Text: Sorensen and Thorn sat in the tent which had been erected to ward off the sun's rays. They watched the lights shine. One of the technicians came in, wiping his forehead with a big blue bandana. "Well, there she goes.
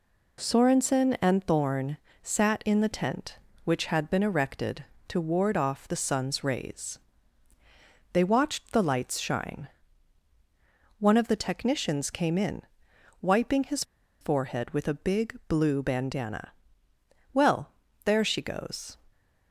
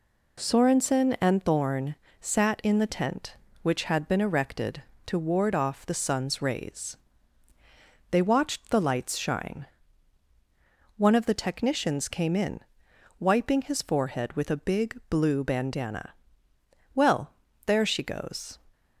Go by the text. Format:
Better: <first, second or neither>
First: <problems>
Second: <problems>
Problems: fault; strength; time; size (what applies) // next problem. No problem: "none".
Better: second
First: pauses between "Thorn" and "sat"; slight; at 1.9 s; 0.26 s long // pauses between "his" and "forehead"; at 13.8 s; 0.37 s long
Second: pauses between "Thorn" and "sat"; slight; at 1.9 s; 0.26 s long